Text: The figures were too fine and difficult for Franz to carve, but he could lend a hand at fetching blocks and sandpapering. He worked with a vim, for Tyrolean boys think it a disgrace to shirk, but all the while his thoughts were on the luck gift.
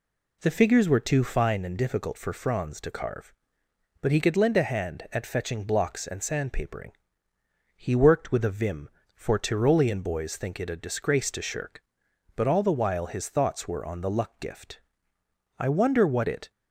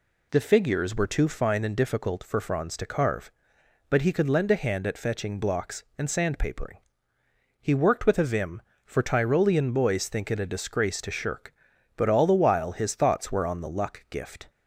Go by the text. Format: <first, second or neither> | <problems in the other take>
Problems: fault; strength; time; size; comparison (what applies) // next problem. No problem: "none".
second | goes on to say "I wonder what it"; noticeable; from 15.5 s on; 0.92 s long